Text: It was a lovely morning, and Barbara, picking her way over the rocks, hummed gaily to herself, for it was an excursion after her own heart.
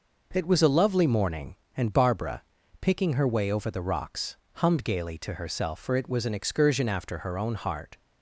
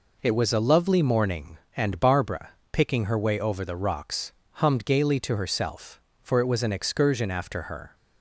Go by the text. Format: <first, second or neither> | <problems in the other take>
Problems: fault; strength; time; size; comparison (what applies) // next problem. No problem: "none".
first | stops before "own heart"; at 7.9 s